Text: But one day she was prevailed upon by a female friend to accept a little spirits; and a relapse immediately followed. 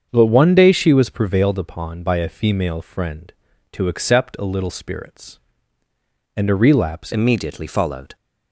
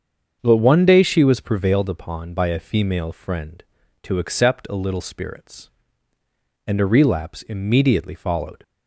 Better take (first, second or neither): second